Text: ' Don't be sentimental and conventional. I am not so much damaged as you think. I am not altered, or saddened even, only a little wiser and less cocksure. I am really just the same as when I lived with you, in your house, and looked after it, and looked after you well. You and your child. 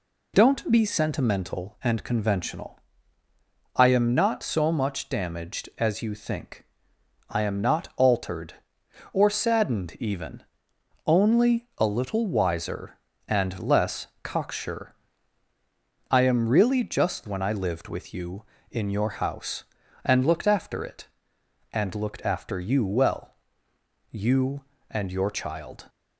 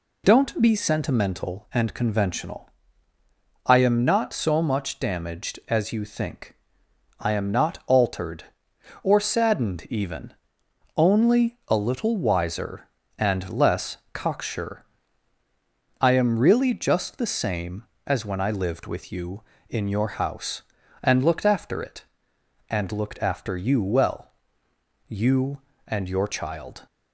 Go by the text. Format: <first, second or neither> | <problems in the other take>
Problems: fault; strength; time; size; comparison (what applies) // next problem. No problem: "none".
second | pauses between "less" and "cocksure"; slight; at 14.0 s; 0.16 s long; slight in the second // skips "the same as"; at 17.2 s